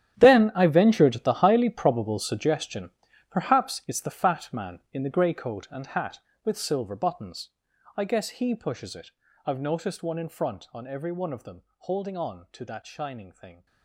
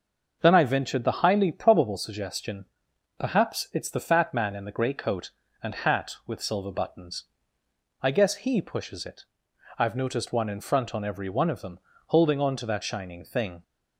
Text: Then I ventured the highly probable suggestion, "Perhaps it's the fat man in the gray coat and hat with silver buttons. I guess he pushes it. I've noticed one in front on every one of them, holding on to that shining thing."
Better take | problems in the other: second | gets quieter; strong; throughout; 16 dB // starts louder than the rest; strong; until 1.1 s; 10.5 dB; also in the second

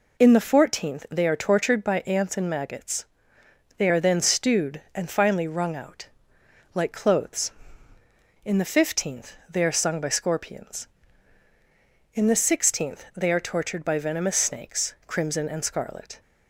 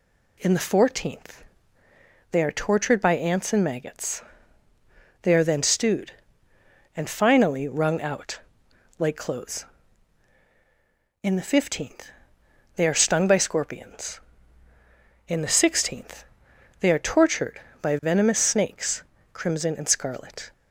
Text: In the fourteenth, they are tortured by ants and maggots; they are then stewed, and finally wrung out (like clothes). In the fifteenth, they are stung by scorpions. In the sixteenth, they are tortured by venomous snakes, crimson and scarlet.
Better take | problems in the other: second | says "sung" for "stung"; at 9.7 s

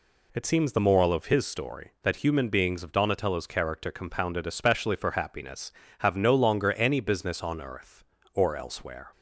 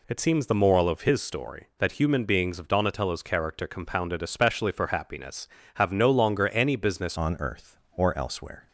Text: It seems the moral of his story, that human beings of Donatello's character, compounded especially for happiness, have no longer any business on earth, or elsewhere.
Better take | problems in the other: first | changes voice at "on"; from 7.1 s on; 1.5 s long

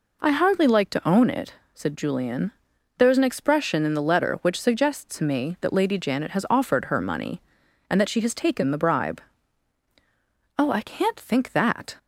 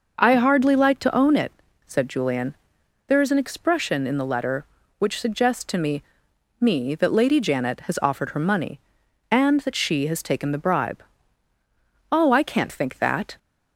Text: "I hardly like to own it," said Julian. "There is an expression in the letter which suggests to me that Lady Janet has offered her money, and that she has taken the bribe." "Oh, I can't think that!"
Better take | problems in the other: first | says "me" twice; at 6.5 s

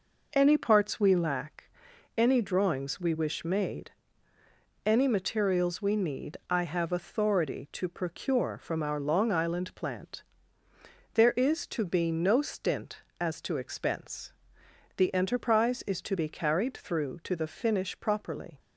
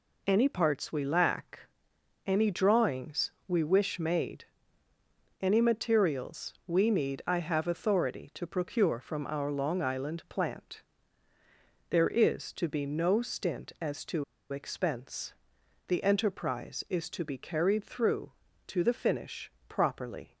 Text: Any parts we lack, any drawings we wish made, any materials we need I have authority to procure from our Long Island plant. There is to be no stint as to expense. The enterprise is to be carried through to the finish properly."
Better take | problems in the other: first | pauses between "to" and "expense"; slight; at 14.2 s; 0.26 s long // pauses between "finish" and "properly"; slight; at 19.5 s; 0.16 s long

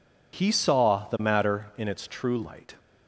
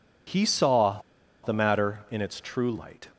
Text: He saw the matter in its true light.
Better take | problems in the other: first | pauses between "saw" and "the"; at 0.9 s; 0.45 s long

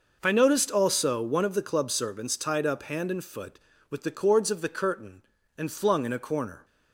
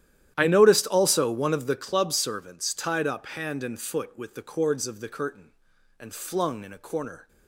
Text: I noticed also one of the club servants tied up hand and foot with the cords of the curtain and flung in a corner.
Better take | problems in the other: first | starts louder than the rest; strong; until 1.8 s; 11.5 dB

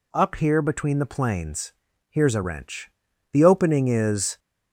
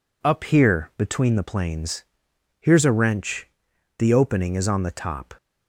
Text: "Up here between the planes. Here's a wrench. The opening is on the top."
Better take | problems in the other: second | stops before "on the top"; at 4.3 s

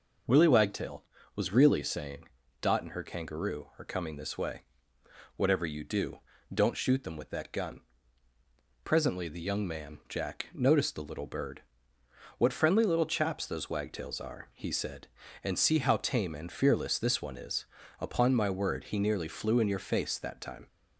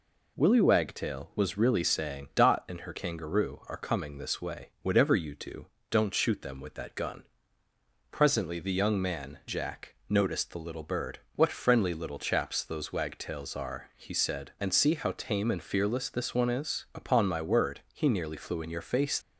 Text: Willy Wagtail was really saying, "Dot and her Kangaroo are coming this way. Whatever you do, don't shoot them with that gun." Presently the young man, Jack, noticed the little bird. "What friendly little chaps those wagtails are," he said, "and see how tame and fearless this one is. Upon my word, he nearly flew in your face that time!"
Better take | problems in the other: first | stops before "that time"; at 19.2 s

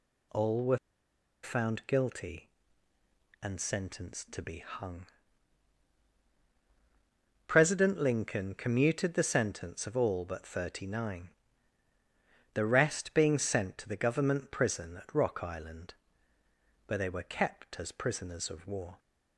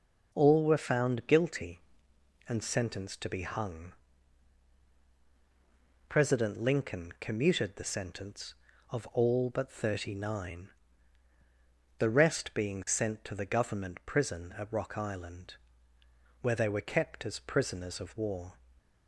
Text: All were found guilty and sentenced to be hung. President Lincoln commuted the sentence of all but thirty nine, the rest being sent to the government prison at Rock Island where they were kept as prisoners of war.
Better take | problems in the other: second | pauses between "were" and "found"; noticeable; at 0.7 s; 0.65 s long // pauses between "Island" and "where"; noticeable; at 15.9 s; 0.92 s long; noticeable in the second

